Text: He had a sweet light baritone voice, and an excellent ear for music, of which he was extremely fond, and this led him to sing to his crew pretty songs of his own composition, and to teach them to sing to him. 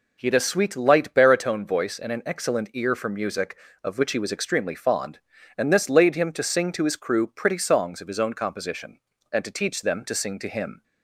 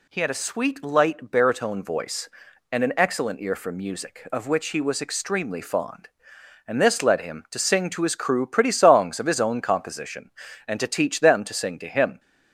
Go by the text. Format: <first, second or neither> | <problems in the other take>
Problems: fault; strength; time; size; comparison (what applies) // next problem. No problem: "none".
second | says "laid" for "led"; at 5.8 s